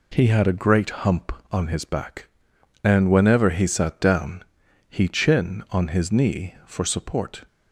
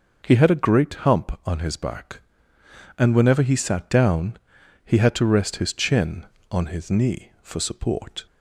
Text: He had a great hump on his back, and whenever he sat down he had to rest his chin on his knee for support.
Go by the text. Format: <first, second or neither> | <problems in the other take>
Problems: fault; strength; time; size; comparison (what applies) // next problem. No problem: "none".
second | pauses between "down" and "he"; at 4.4 s; 0.42 s long; noticeable in the second // skips "had to rest his"; at 5.0 s